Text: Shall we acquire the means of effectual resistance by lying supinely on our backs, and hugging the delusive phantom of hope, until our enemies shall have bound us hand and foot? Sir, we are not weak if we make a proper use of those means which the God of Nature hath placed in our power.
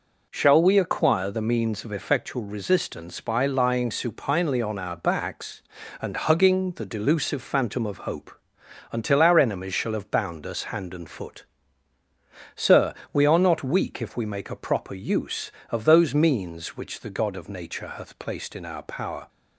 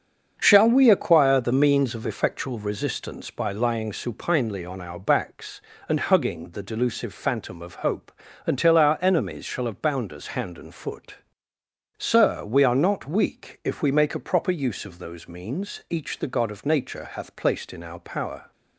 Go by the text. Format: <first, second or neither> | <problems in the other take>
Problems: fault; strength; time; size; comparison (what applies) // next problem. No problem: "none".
first | starts louder than the rest; until 1.4 s; 7 dB // says "each" for "which"; at 15.8 s